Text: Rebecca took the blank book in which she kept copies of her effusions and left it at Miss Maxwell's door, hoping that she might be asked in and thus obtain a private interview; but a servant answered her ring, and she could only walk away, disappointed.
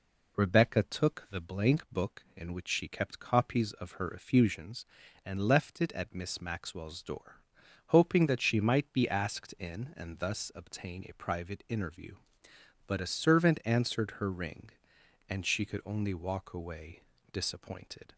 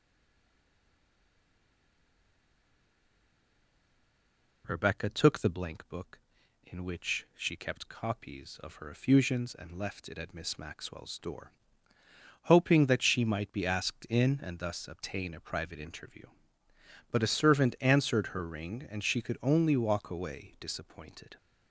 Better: first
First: none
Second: stays silent before the first word; strong; until 4.6 s; 4.6 s long

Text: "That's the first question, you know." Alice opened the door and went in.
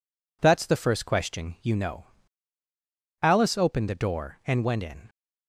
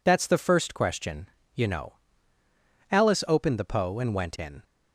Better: first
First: none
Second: says "poe" for "door"; at 3.6 s

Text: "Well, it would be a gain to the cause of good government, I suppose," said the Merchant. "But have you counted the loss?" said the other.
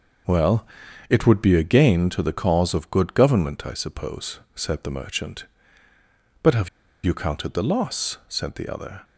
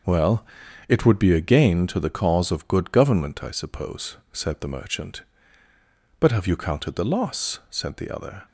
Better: second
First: pauses between "have" and "you"; at 6.6 s; 0.37 s long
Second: none

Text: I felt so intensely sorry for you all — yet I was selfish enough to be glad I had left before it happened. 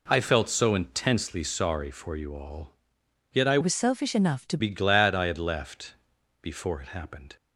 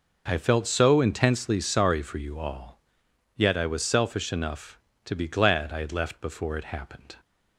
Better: second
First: changes voice from "was" to "to"; from 3.6 to 4.5 s; 0.9 s long // pauses between "left" and "before"; noticeable; at 5.9 s; 0.48 s long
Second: none

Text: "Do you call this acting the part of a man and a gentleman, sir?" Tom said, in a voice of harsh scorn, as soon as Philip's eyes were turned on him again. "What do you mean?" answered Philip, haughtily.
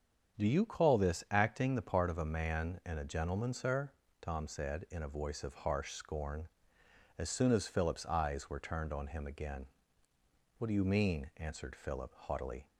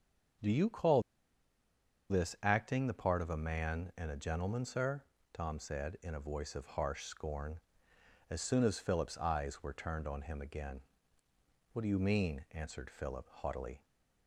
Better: first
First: starts louder than the rest; strong; until 1.4 s; 7.5 dB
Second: starts louder than the rest; strong; until 2.5 s; 7.5 dB // pauses between "call" and "this"; at 1.0 s; 1.0 s long

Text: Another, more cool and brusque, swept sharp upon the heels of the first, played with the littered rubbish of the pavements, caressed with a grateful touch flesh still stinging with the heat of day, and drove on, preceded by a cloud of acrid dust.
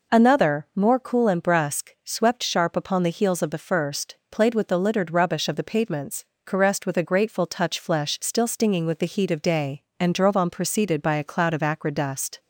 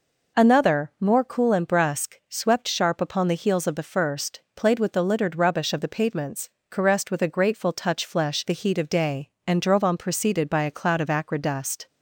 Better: first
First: none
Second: skips "still stinging with"; at 8.4 s

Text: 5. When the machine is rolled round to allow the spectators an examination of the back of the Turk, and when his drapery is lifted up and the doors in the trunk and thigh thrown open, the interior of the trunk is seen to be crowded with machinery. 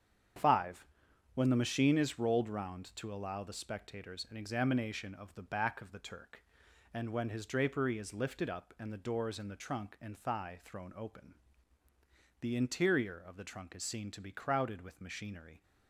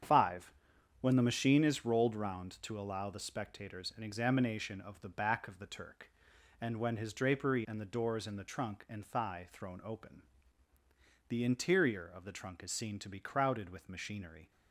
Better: first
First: starts louder than the rest; strong; until 1.8 s; 8 dB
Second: starts louder than the rest; strong; until 1.5 s; 8 dB // skips "is lifted up"; at 7.6 s

